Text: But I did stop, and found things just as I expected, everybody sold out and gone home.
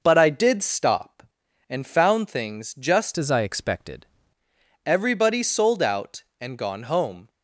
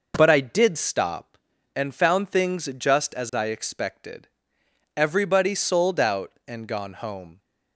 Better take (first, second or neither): second